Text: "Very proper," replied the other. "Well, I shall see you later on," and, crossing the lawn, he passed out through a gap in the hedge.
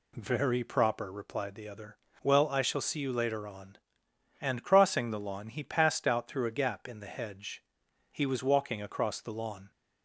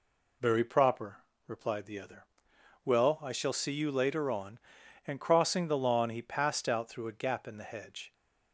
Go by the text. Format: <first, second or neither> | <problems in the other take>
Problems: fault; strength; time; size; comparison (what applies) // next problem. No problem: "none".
second | goes on to say "He was walking across the lawn"; from 8.1 s on; 1.5 s long